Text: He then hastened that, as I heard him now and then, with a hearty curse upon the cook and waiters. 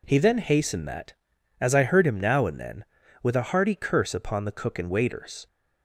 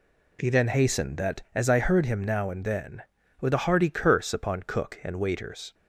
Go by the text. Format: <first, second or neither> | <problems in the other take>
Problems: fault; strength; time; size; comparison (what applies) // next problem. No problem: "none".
first | skips "the"; at 4.6 s